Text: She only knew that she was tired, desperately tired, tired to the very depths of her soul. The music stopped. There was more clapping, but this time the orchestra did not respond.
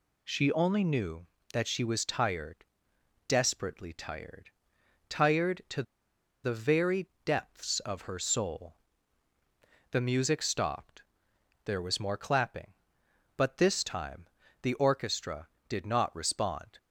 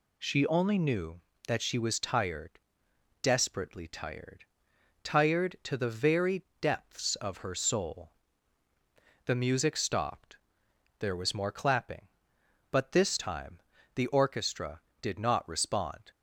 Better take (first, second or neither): second